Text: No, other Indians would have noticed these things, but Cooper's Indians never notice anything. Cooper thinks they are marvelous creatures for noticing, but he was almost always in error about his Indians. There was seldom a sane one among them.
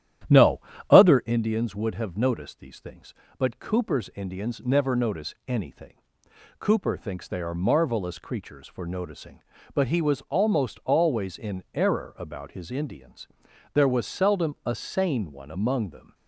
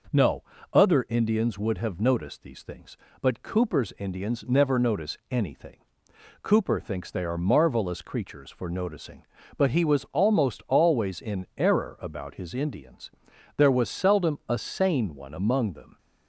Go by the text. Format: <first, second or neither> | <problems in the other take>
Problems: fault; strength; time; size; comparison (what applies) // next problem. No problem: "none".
second | starts louder than the rest; strong; until 1.4 s; 11 dB